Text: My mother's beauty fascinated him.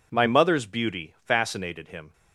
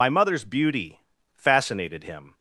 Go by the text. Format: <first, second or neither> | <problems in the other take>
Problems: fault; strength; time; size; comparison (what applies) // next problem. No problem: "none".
first | loses the start of "My"; at 0.0 s; 55 ms // pauses between "beauty" and "fascinated"; at 0.9 s; 0.37 s long